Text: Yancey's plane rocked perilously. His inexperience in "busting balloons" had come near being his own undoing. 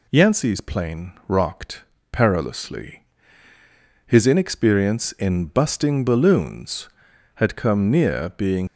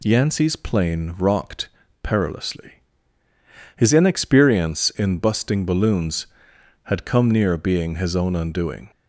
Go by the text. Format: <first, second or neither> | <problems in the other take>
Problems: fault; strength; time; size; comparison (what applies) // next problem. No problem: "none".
second | pauses between "plane" and "rocked"; slight; at 1.1 s; 0.16 s long // pauses between "rocked" and "perilously"; slight; at 1.8 s; 0.30 s long; slight in the second // stops before "his own undoing"; at 8.6 s